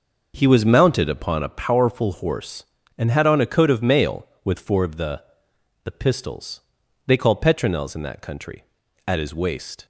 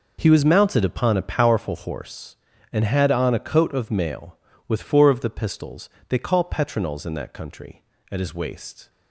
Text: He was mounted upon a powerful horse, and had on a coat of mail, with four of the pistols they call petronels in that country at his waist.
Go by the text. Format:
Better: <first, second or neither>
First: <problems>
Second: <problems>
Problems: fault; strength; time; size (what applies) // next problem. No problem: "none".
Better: second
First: says "the" twice; at 5.8 s // pauses between "pistols" and "they"; noticeable; at 6.5 s; 0.48 s long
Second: pauses between "pistols" and "they"; slight; at 5.8 s; 0.22 s long